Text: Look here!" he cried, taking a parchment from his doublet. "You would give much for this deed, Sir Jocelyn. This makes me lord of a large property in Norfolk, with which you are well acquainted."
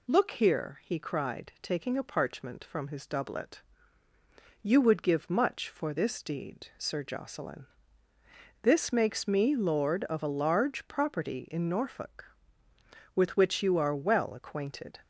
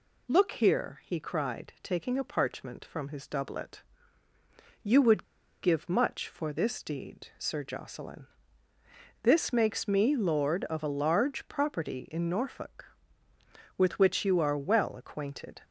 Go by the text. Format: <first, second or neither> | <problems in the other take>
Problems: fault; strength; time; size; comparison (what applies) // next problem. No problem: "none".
first | pauses between "would" and "give"; at 5.2 s; 0.38 s long